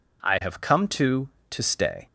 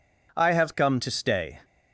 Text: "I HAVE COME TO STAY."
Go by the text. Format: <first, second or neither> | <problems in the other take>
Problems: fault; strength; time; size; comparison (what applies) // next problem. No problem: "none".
second | says "TO" twice; at 1.5 s